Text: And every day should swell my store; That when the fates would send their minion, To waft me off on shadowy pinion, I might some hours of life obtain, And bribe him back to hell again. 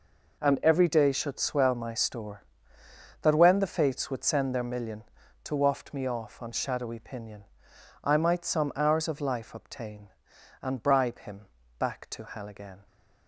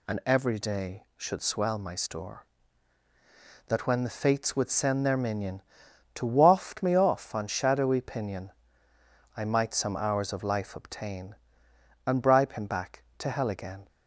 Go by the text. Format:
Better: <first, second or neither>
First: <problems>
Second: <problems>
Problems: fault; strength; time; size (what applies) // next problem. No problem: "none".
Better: second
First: says "million" for "minion"; at 4.6 s // pauses between "him" and "back"; slight; at 11.4 s; 0.32 s long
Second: none